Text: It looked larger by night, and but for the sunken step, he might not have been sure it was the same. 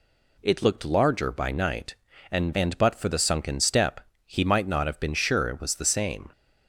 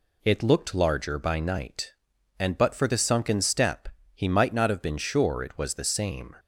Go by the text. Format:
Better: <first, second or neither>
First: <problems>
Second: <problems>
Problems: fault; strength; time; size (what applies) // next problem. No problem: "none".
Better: second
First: says "and" twice; at 2.5 s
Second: none